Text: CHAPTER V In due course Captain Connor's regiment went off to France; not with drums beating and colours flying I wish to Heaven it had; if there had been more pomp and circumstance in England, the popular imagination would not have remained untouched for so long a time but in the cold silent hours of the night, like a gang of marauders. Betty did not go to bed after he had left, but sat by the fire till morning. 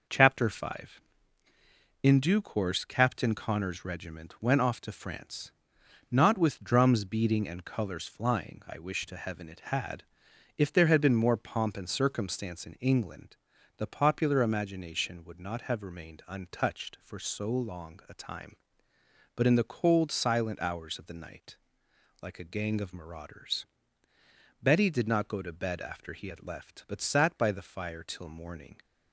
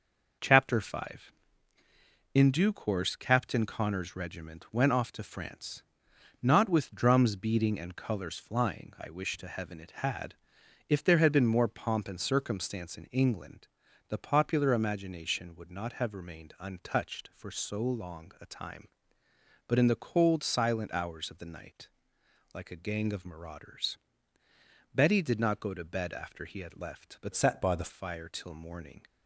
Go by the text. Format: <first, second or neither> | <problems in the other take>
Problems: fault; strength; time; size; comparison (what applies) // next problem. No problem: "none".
first | changes voice from "sat" to "the"; from 27.3 to 27.8 s; 0.5 s long